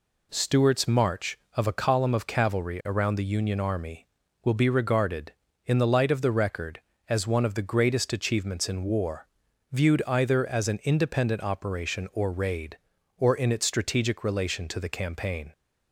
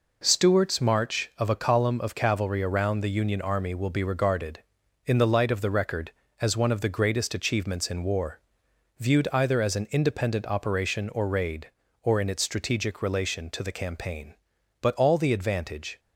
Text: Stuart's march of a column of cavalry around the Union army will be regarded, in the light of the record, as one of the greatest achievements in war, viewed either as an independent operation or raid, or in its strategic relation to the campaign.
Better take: first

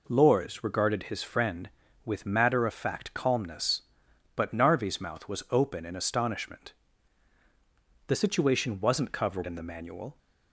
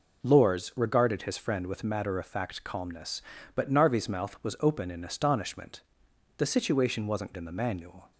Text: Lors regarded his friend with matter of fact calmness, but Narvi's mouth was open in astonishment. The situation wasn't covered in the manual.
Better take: first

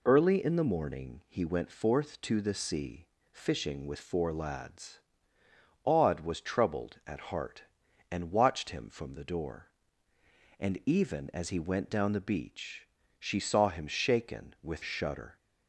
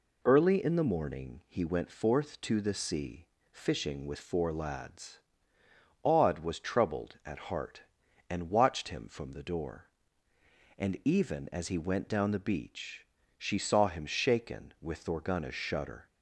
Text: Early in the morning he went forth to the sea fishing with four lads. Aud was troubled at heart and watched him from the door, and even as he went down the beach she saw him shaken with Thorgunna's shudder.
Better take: second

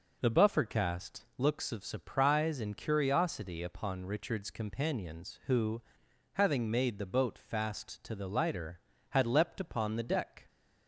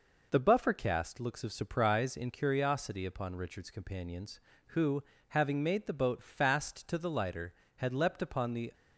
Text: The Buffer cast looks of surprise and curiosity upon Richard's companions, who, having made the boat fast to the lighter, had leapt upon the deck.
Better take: first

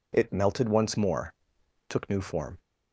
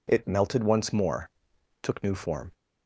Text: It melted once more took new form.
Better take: neither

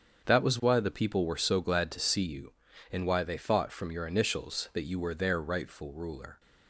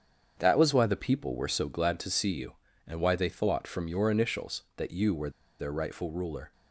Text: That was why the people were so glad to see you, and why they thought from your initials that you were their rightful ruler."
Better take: first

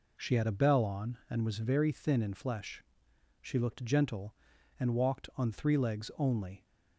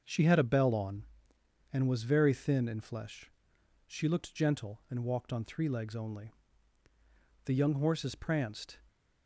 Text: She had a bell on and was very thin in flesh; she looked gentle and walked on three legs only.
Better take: first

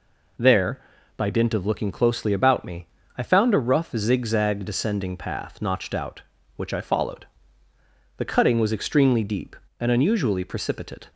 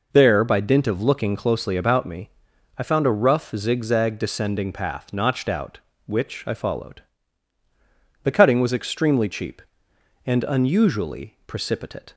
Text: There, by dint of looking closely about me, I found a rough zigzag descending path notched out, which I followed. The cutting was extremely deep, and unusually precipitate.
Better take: first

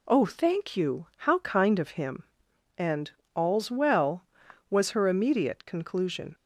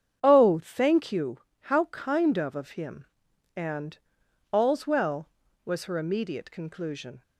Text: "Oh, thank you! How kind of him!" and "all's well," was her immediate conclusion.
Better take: first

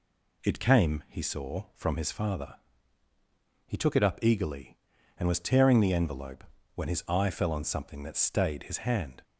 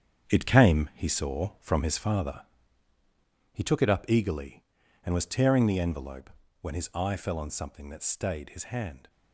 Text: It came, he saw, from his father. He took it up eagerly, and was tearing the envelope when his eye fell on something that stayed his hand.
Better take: first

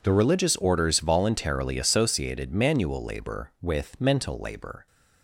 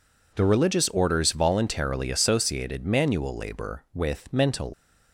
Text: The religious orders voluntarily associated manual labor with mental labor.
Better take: first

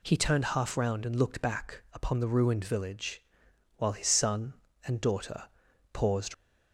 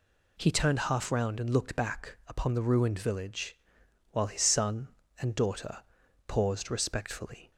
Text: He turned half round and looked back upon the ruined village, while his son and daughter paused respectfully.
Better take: second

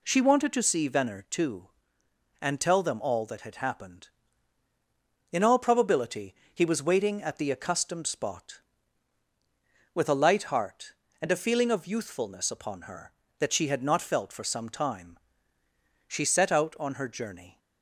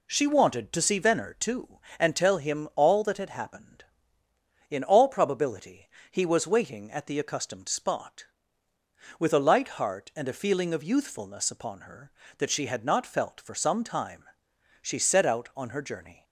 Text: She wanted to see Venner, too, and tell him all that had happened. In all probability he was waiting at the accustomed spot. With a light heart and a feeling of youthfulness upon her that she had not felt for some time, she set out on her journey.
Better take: second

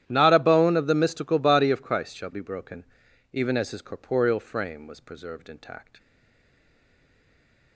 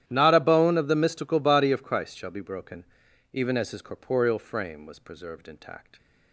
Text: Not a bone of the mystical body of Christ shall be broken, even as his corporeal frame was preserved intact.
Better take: second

